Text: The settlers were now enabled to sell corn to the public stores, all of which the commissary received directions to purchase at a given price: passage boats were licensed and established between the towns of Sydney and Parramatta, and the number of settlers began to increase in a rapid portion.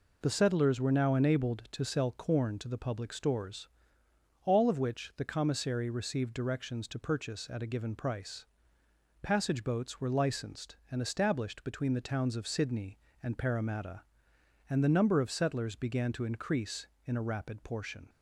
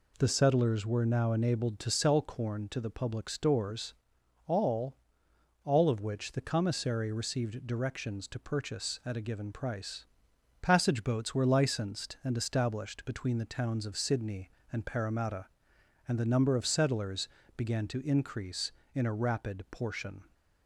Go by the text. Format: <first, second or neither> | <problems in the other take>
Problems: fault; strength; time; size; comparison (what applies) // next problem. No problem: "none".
first | says "all" twice; at 5.6 s // pauses between "settlers" and "began"; slight; at 17.2 s; 0.30 s long